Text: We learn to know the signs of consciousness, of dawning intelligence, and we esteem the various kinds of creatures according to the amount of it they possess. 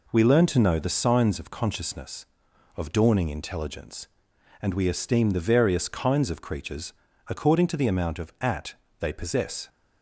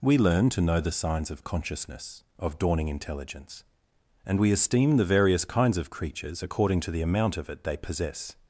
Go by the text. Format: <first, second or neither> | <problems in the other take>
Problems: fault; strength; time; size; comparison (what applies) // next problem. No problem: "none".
second | pauses between "creatures" and "according"; slight; at 6.9 s; 0.34 s long // says "at" for "it"; at 8.3 s